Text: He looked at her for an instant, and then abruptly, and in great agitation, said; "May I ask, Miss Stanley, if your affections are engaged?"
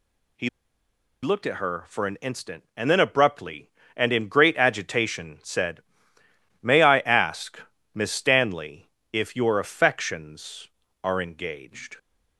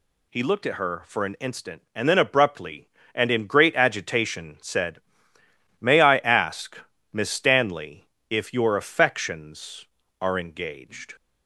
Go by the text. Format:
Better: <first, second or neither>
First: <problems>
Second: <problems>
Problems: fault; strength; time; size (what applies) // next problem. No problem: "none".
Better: second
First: pauses between "He" and "looked"; noticeable; at 0.4 s; 0.74 s long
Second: none